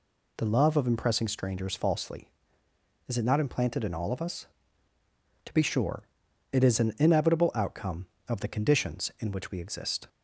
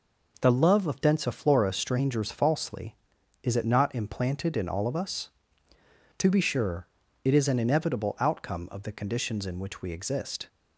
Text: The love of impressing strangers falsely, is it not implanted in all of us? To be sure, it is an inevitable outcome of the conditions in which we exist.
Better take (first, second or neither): first